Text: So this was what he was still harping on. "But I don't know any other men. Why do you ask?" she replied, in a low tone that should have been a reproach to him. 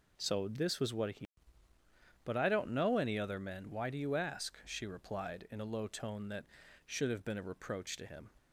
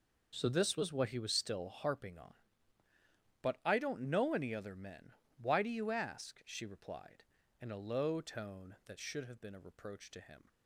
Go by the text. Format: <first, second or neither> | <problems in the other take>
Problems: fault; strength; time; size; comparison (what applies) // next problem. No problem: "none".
second | skips "was still harping on"; at 1.7 s